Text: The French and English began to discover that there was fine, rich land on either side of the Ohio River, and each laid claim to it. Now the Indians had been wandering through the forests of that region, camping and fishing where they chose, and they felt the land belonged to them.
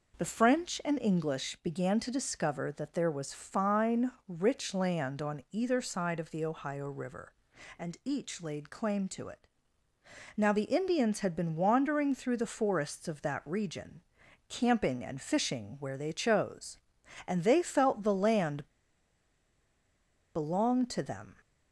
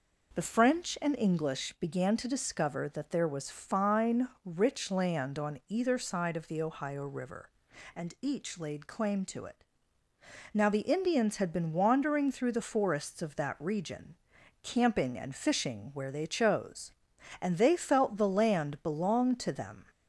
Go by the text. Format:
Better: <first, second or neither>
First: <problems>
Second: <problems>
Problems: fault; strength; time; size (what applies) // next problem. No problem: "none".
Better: second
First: pauses between "land" and "belonged"; strong; at 18.6 s; 1.6 s long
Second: none